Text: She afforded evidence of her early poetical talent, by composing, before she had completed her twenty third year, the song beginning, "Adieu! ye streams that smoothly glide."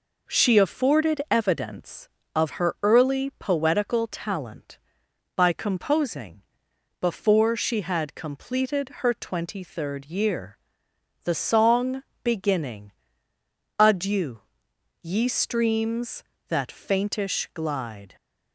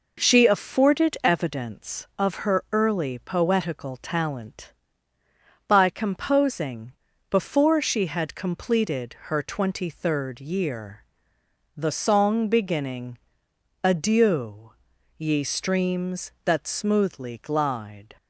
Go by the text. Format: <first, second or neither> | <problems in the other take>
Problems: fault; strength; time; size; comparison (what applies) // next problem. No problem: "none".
second | pauses between "song" and "beginning"; slight; at 12.0 s; 0.20 s long // says "faintish" for "smoothly"; at 16.7 s